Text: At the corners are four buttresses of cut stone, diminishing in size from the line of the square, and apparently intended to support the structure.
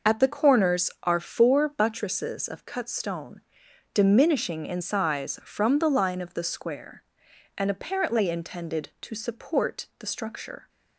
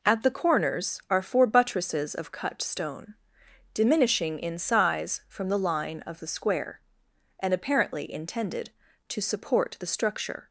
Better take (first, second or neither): second